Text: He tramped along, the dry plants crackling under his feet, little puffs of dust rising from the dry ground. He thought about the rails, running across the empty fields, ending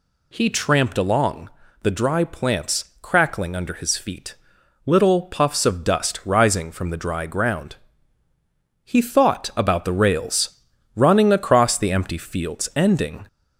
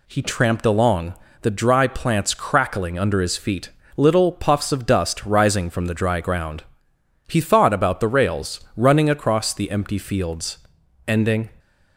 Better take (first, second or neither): second